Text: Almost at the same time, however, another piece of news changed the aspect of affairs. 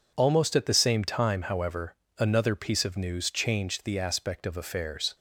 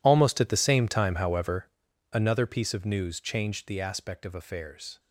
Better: first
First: none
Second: gets quieter; strong; throughout; 18 dB

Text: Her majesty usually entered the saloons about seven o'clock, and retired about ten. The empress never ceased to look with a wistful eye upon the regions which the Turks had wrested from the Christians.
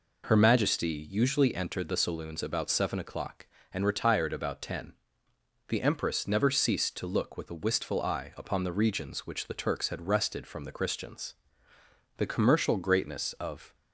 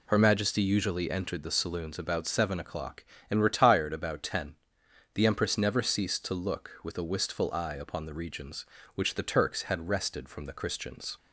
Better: second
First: goes on to say "The commercial greatness of"; from 12.1 s on; 1.5 s long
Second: none

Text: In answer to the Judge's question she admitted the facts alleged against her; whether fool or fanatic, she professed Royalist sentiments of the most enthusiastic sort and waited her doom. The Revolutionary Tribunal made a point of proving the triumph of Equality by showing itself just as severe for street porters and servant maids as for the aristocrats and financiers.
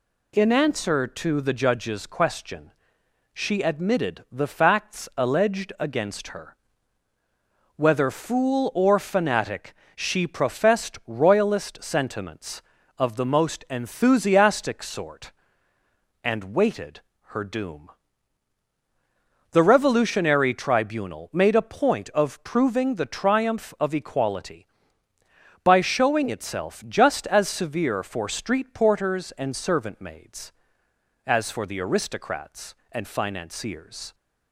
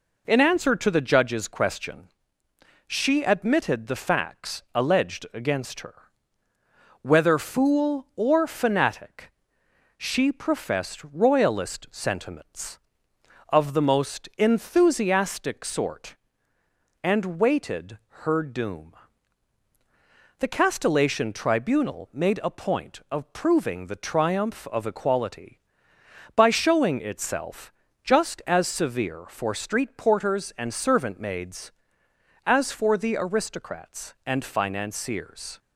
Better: first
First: pauses between "question" and "she"; noticeable; at 2.7 s; 0.60 s long // pauses between "waited" and "her"; slight; at 16.9 s; 0.28 s long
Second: pauses between "question" and "she"; noticeable; at 2.0 s; 0.80 s long // pauses between "waited" and "her"; slight; at 17.9 s; 0.24 s long // says "Castellation" for "Revolutionary"; at 20.4 s // pauses between "itself" and "just"; slight; at 27.7 s; 0.32 s long

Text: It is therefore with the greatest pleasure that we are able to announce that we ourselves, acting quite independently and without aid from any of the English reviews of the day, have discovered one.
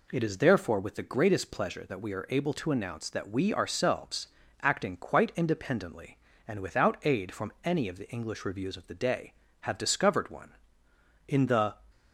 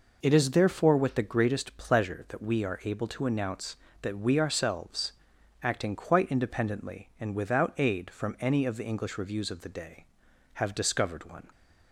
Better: second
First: goes on to say "In the"; from 11.2 s on; 0.52 s long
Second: none

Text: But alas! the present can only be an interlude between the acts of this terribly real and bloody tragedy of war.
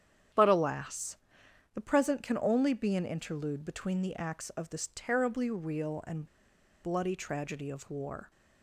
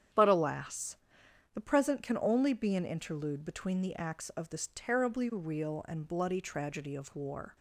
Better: second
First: starts louder than the rest; strong; until 1.9 s; 8.5 dB // pauses between "and" and "bloody"; noticeable; at 6.2 s; 0.57 s long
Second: starts louder than the rest; strong; until 1.7 s; 8.5 dB

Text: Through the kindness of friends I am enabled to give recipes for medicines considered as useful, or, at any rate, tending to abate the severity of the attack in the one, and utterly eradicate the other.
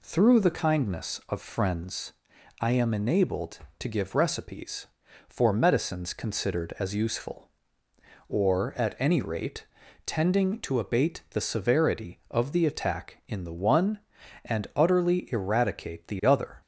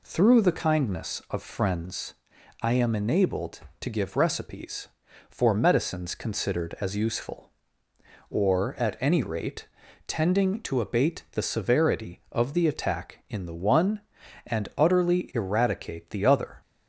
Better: neither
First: pauses between "friends" and "I"; noticeable; at 2.1 s; 0.46 s long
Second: pauses between "friends" and "I"; noticeable; at 2.1 s; 0.46 s long

